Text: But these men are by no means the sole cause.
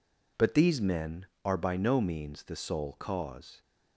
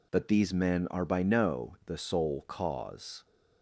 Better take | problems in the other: first | skips "means"; at 1.8 s

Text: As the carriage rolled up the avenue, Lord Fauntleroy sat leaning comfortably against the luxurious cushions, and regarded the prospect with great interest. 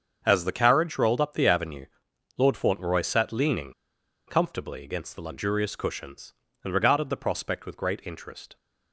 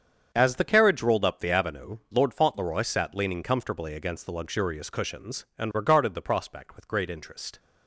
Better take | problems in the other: second | starts louder than the rest; until 1.2 s; 7 dB; strong in the second // pauses between "leaning" and "comfortably"; noticeable; at 3.7 s; 0.55 s long

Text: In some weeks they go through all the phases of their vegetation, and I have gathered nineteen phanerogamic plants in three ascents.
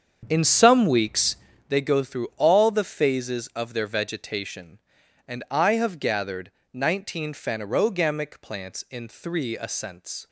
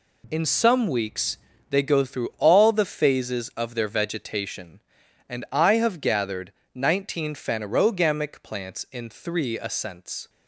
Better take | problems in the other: second | starts louder than the rest; strong; until 1.7 s; 7.5 dB // pauses between "weeks" and "they"; slight; at 1.3 s; 0.32 s long; slight in the second // pauses between "gathered" and "nineteen"; slight; at 6.4 s; 0.22 s long; slight in the second

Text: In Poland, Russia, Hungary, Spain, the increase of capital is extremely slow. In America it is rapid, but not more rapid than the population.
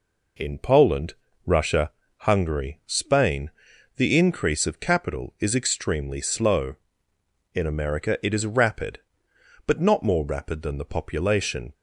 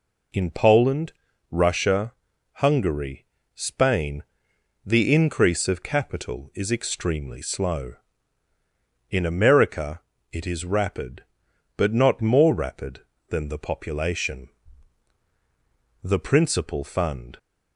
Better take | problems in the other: first | pauses between "America" and "it"; slight; at 10.0 s; 0.30 s long // goes on to say "The principal fund"; from 16.0 s on; 1.3 s long

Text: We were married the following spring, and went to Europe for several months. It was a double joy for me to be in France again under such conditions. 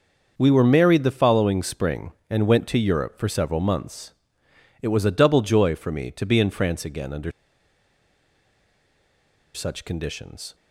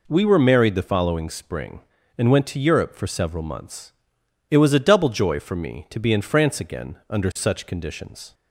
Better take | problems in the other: second | starts louder than the rest; until 1.3 s; 6.5 dB // pauses between "under" and "such"; strong; at 7.3 s; 2.2 s long

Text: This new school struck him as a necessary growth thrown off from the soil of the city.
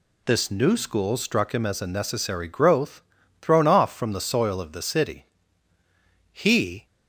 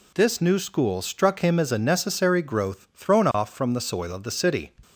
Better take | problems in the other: second | pauses between "growth" and "thrown"; at 3.0 s; 0.40 s long // goes on to say "He"; from 6.3 s on; 0.54 s long

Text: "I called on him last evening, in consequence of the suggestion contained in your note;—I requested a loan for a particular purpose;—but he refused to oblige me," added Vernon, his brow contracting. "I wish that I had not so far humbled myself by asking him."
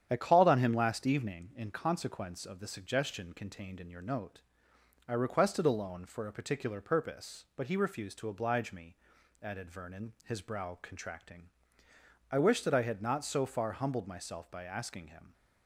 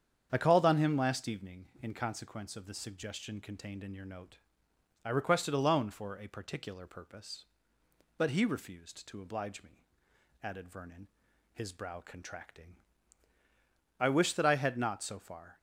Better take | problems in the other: first | starts louder than the rest; strong; until 1.3 s; 8 dB; strong in the first // stops before "humbled myself by asking him"; at 15.5 s

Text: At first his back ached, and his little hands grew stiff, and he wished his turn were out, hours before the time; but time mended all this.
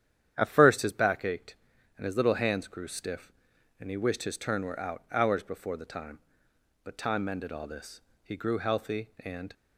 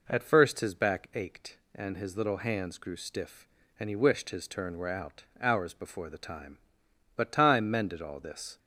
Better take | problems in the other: second | starts louder than the rest; strong; until 1.3 s; 10 dB // goes on to say "He grew healthy and"; noticeable; from 8.2 s on; 1.3 s long

